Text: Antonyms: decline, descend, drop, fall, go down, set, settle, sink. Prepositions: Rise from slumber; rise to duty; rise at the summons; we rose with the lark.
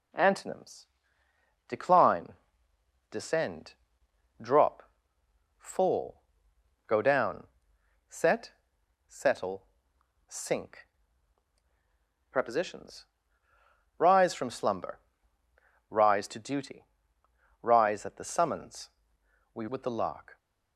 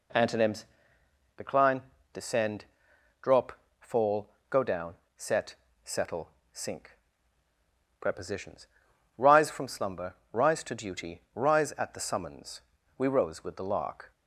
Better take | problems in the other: second | skips "rose"; at 19.6 s

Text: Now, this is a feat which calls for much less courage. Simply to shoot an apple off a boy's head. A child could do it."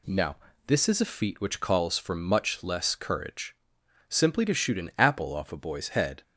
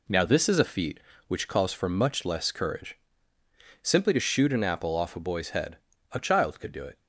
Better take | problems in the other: second | stops before "A child could do it"; at 6.2 s

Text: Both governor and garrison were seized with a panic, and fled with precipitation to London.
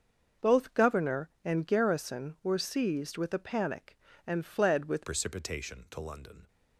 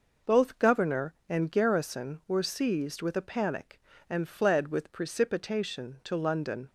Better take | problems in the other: second | starts louder than the rest; until 1.5 s; 6.5 dB // changes voice at "precipitation"; from 5.0 s on; 1.4 s long

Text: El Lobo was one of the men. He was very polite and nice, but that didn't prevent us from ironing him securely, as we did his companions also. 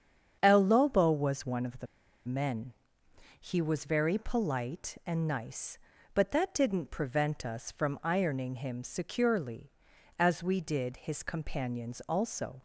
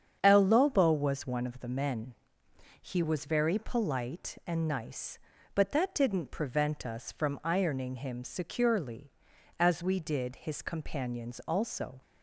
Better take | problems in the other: second | starts louder than the rest; strong; until 1.4 s; 7.5 dB; strong in the second // pauses between "the" and "men"; at 1.8 s; 0.42 s long

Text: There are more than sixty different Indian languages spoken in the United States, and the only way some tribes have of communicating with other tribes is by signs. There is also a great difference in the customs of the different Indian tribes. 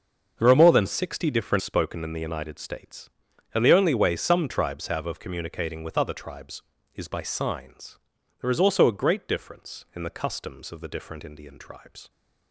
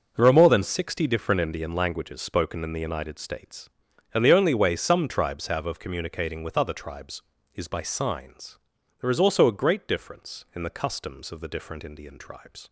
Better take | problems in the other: second | starts louder than the rest; until 1.3 s; 6.5 dB // skips "Indian languages"; at 1.6 s

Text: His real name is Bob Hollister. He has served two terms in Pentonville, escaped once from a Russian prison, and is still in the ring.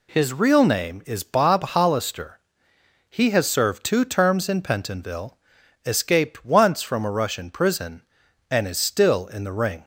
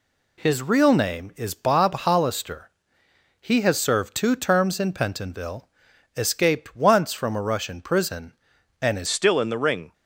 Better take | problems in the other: first | changes voice at "still"; from 9.0 s on; 0.9 s long

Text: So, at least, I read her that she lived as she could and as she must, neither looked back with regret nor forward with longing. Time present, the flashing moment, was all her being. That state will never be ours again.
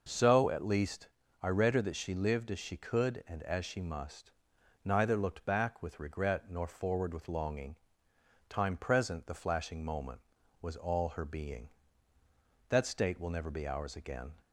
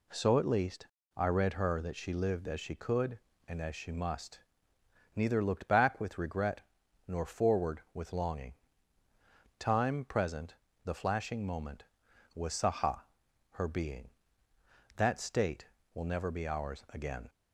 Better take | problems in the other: first | pauses between "regret" and "nor"; noticeable; at 6.6 s; 0.46 s long // says "saha" for "all"; at 12.5 s

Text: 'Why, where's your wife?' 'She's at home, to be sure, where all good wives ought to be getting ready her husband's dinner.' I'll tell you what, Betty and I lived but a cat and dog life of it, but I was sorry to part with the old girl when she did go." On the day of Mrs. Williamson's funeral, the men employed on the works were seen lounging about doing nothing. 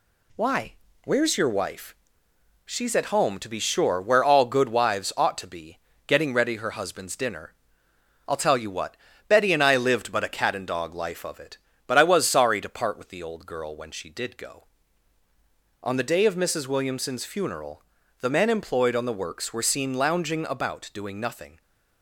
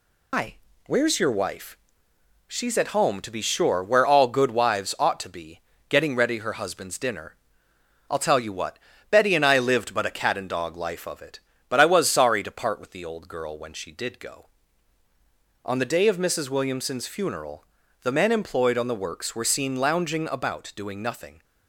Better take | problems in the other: first | loses the start of "Why"; at 0.3 s; 200 ms // pauses between "be" and "getting"; slight; at 5.6 s; 0.28 s long; slight in the first

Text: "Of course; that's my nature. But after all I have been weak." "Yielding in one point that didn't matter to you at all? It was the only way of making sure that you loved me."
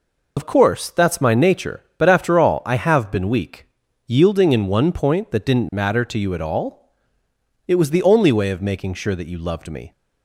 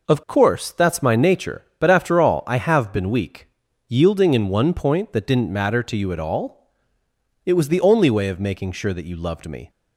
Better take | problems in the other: second | loses the start of "Of"; at 0.3 s; 65 ms

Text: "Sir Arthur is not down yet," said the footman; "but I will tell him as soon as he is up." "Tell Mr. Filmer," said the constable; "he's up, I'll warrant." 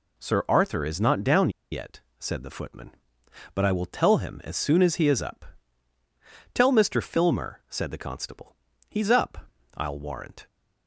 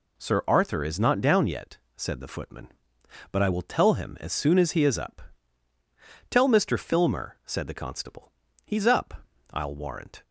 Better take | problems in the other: second | pauses between "down" and "yet"; slight; at 1.5 s; 0.21 s long

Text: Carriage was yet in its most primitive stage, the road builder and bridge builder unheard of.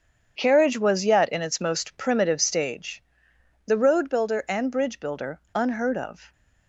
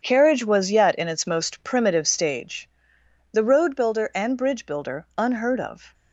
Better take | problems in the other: neither | starts louder than the rest; strong; the same in both

